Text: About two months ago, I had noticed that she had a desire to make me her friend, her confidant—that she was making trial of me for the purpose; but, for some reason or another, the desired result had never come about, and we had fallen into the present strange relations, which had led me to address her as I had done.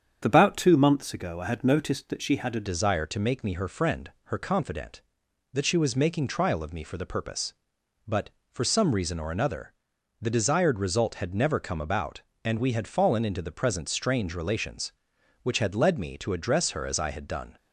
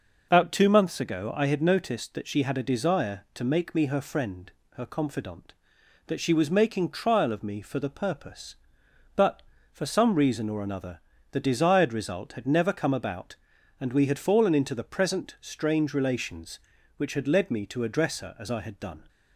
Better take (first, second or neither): second